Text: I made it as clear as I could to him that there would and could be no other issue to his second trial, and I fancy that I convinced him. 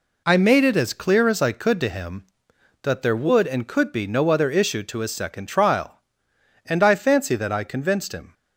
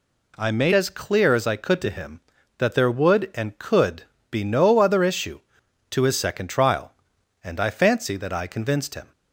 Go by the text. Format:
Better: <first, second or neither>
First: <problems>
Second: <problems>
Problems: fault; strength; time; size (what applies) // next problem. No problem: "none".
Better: first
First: none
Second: skips "it"; at 0.7 s // pauses between "could" and "be"; slight; at 4.0 s; 0.26 s long